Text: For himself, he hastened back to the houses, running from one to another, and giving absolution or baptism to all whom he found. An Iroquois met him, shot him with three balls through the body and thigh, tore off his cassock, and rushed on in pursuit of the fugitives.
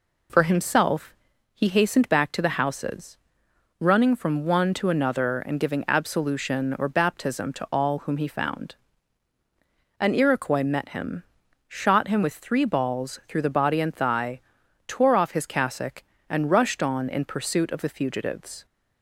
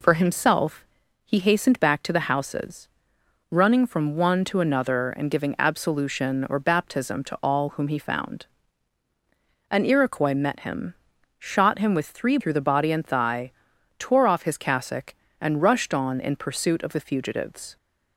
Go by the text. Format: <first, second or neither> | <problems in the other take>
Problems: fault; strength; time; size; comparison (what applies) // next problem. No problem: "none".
first | skips "balls"; at 12.3 s